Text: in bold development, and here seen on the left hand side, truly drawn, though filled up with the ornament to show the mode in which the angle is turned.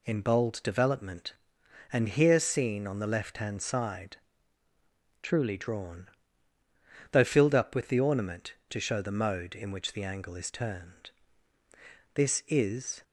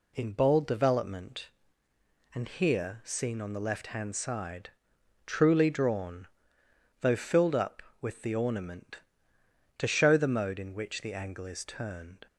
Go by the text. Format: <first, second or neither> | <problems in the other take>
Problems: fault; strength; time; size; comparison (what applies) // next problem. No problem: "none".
second | goes on to say "This is"; noticeable; from 12.1 s on; 0.88 s long